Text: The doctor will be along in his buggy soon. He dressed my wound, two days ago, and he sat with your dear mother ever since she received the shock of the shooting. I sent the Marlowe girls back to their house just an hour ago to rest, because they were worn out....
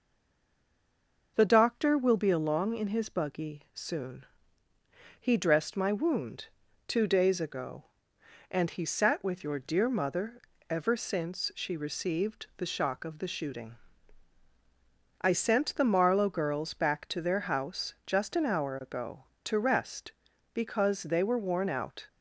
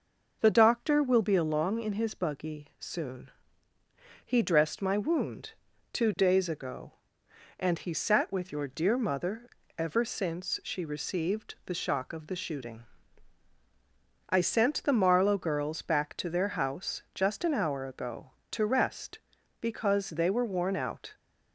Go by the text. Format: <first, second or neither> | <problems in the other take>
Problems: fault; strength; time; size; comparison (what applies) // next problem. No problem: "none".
second | stays silent before the first word; noticeable; until 1.3 s; 1.3 s long // pauses between "mother" and "ever"; slight; at 10.3 s; 0.30 s long; slight in the second